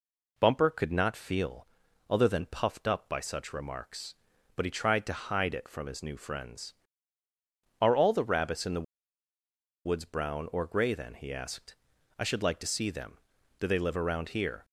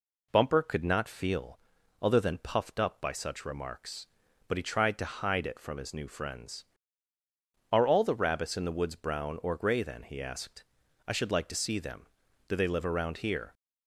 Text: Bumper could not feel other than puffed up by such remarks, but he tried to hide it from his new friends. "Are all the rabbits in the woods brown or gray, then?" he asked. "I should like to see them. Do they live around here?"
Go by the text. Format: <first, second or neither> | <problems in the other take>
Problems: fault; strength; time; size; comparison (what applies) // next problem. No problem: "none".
second | pauses between "feel" and "other"; at 1.6 s; 0.42 s long; also in the second // pauses between "the" and "woods"; at 8.8 s; 1.0 s long